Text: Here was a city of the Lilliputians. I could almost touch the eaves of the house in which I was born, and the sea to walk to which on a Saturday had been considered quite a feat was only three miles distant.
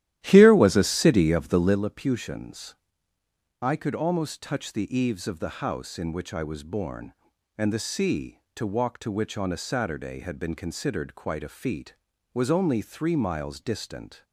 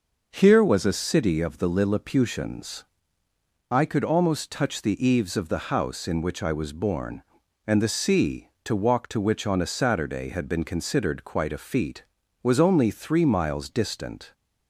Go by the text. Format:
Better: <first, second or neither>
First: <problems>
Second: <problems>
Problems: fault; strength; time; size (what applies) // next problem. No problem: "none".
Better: second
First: starts louder than the rest; strong; until 1.8 s; 13 dB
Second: none